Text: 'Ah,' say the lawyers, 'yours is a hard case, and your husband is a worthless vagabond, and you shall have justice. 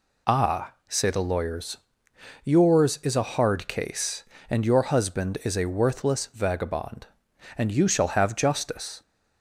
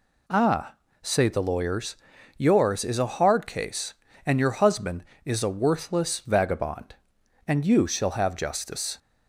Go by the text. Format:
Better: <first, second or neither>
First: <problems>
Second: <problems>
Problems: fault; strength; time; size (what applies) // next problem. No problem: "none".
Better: neither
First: none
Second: none